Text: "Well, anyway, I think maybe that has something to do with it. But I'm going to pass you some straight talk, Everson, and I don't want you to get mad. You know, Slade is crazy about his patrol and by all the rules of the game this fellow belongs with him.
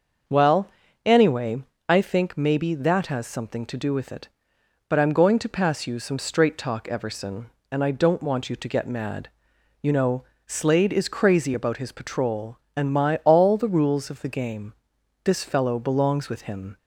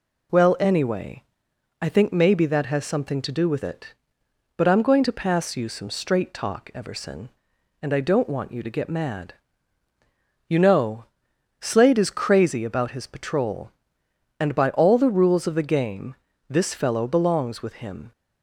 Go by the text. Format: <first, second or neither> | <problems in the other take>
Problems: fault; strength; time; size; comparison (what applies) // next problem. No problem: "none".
second | starts louder than the rest; until 1.9 s; 6.5 dB // says "my" for "by"; at 12.9 s // pauses between "game" and "this"; noticeable; at 14.7 s; 0.52 s long; slight in the second